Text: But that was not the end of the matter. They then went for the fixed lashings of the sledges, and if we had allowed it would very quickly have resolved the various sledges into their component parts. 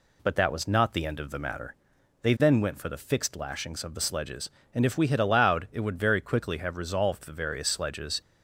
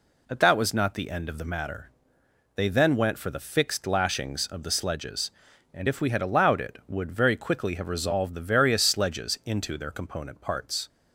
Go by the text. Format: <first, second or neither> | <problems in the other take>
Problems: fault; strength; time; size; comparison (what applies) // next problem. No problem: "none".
second | stops before "into their component parts"; at 8.2 s